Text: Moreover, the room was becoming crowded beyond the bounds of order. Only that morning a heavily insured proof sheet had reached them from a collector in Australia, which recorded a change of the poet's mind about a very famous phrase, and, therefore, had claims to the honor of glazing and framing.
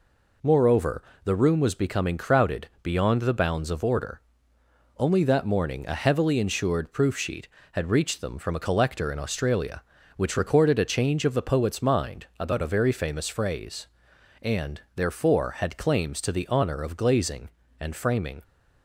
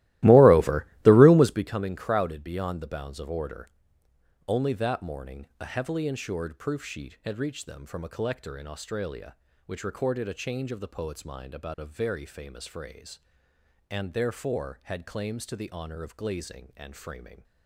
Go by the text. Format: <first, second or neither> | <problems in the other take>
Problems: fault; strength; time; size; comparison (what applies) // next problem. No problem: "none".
first | starts louder than the rest; strong; until 1.7 s; 17 dB